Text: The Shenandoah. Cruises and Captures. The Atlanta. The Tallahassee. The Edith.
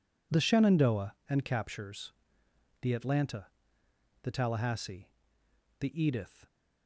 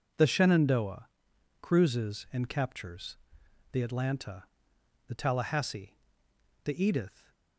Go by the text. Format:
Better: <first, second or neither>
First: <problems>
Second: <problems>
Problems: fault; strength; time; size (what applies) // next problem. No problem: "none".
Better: second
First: skips "Cruises"; at 1.2 s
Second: none